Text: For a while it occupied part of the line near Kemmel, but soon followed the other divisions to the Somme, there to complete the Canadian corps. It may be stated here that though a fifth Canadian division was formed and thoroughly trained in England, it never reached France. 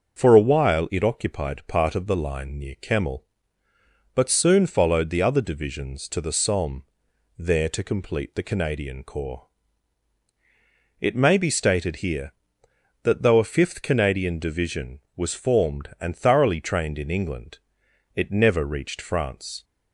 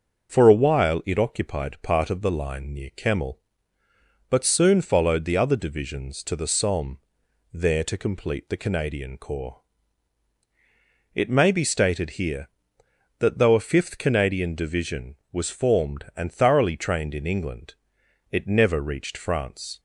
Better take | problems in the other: neither | starts louder than the rest; the same in both

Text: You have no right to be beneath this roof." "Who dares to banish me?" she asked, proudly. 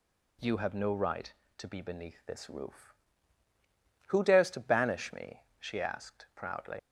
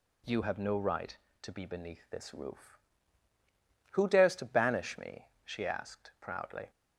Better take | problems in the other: second | leaves "proudly" unfinished; at 6.7 s; 55 ms

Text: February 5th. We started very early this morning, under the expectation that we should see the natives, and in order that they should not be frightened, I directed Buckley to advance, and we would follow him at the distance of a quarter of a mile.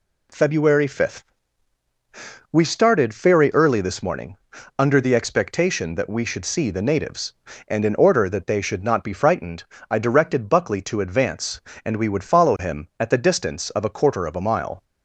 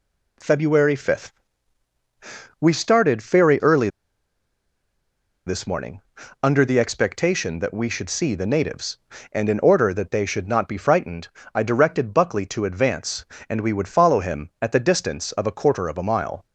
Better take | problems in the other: first | pauses between "early" and "this"; strong; at 3.8 s; 1.5 s long

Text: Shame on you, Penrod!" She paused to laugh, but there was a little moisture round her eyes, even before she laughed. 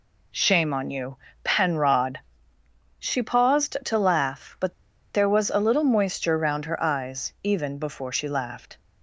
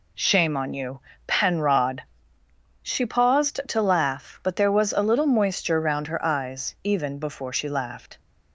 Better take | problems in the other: second | pauses between "but" and "there"; at 4.7 s; 0.42 s long

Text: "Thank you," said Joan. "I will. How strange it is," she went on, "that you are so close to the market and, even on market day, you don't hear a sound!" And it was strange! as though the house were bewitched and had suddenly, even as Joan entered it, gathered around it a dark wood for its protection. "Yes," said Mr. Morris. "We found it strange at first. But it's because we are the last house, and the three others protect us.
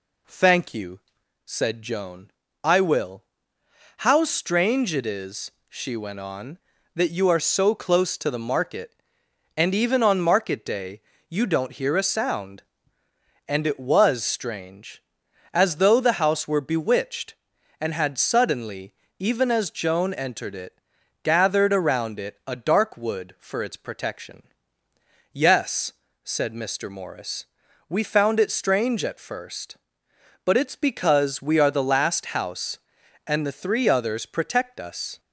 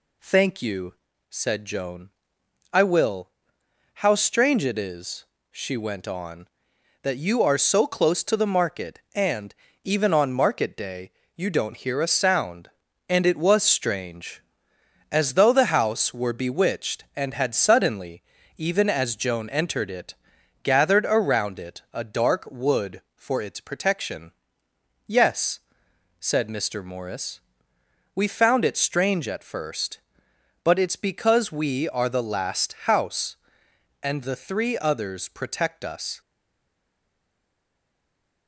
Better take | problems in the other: first | stays silent after the last word; from 36.2 s on; 2.2 s long

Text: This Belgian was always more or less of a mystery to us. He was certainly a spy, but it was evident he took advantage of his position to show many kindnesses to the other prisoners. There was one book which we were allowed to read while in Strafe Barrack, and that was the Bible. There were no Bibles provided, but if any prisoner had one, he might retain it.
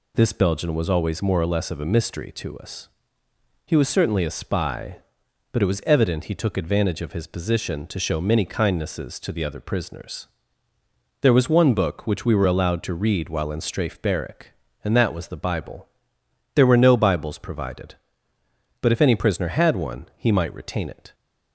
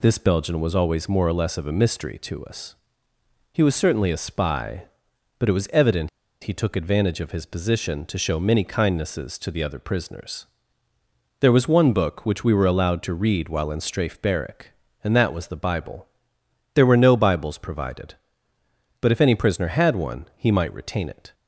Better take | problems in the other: first | pauses between "evident" and "he"; slight; at 6.0 s; 0.34 s long

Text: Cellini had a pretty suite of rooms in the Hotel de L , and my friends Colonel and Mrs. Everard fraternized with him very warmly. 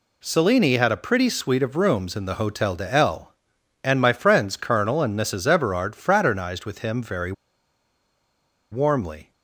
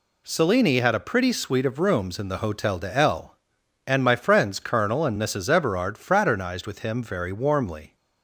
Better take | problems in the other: second | pauses between "very" and "warmly"; strong; at 7.3 s; 1.3 s long

